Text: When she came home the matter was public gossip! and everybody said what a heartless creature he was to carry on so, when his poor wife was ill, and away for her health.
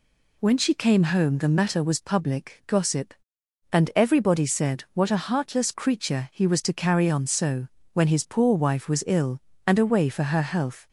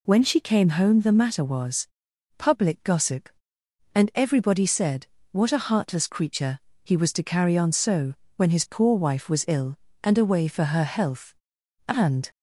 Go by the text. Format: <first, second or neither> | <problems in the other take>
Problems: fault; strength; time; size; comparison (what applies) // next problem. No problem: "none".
first | pauses between "was" and "public"; noticeable; at 1.8 s; 0.50 s long // pauses between "said" and "what"; slight; at 5.0 s; 0.24 s long // pauses between "creature" and "he"; slight; at 6.6 s; 0.24 s long // goes on to say "And"; slight; from 11.8 s on; 0.42 s long